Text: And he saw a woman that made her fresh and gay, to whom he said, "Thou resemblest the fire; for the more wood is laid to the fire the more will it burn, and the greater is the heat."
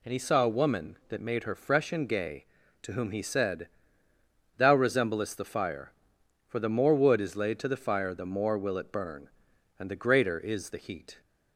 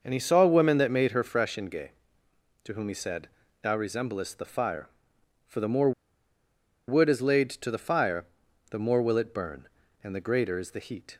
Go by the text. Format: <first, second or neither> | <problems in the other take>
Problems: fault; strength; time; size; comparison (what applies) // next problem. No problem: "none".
first | pauses between "more" and "wood"; noticeable; at 5.9 s; 0.96 s long // pauses between "fire" and "the"; noticeable; at 8.2 s; 0.46 s long